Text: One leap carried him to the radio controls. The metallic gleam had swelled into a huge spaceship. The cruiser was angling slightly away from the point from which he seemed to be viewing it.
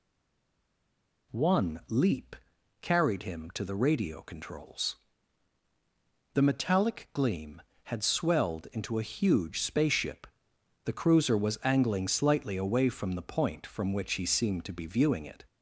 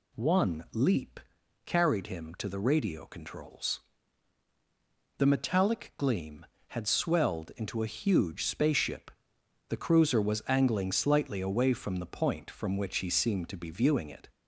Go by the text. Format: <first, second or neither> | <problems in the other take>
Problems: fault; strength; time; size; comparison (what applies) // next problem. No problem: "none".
second | stays silent before the first word; noticeable; until 1.3 s; 1.3 s long // pauses between "leap" and "carried"; noticeable; at 2.3 s; 0.46 s long; noticeable in the second